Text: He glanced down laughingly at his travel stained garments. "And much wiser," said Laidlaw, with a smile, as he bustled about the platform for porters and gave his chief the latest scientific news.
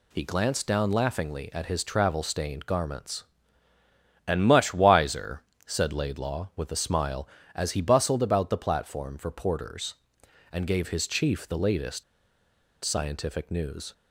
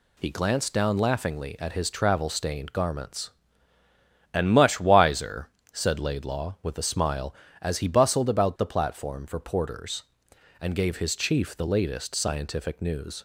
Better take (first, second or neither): second